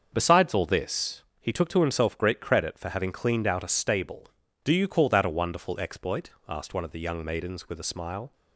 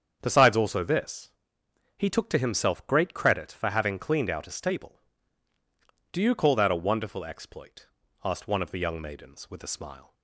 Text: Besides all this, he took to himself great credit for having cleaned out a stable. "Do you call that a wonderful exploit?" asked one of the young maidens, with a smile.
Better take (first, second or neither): first